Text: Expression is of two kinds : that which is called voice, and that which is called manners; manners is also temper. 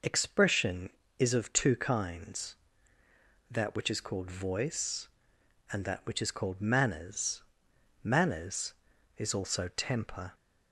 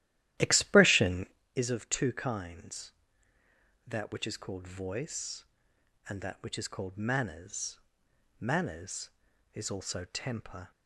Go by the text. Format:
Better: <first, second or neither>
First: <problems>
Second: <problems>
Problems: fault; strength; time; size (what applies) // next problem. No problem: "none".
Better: first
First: none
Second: starts louder than the rest; strong; until 1.4 s; 13 dB